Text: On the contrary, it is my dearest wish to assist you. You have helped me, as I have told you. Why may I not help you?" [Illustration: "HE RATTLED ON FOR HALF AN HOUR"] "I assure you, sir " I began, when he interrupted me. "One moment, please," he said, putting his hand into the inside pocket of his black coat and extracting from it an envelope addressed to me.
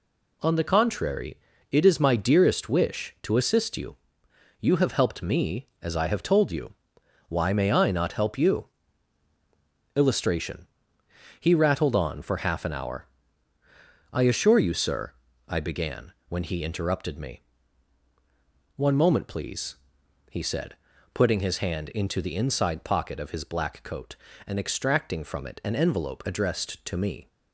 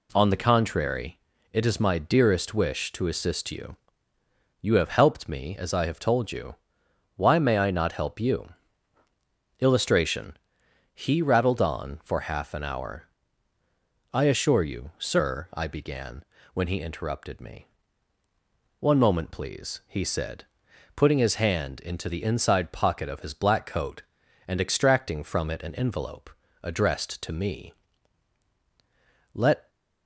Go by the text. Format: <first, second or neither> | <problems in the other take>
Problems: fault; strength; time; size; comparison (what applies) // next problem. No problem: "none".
first | pauses between "HOUR" and "I"; at 13.0 s; 1.0 s long; also in the first // pauses between "envelope" and "addressed"; slight; at 26.3 s; 0.34 s long // goes on to say "Let"; slight; from 29.3 s on; 0.36 s long